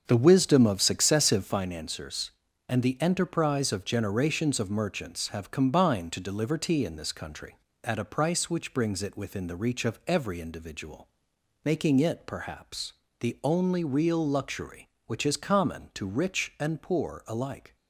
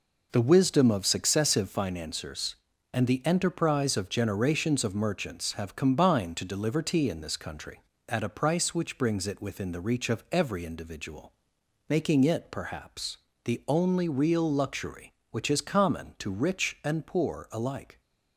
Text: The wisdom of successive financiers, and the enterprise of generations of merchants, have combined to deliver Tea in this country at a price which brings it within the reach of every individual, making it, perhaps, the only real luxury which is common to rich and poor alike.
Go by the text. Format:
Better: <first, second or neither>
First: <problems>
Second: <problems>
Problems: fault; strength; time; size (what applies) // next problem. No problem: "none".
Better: second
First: starts louder than the rest; until 1.7 s; 7 dB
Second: none